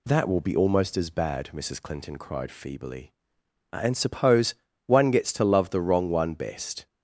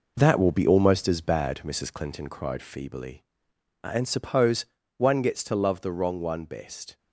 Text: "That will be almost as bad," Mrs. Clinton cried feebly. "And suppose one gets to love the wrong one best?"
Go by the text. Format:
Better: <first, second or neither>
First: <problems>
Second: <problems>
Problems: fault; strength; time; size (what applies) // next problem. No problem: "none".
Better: first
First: pauses between "suppose" and "one"; slight; at 4.5 s; 0.32 s long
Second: gets quieter; strong; throughout; 7.5 dB // pauses between "suppose" and "one"; slight; at 4.6 s; 0.32 s long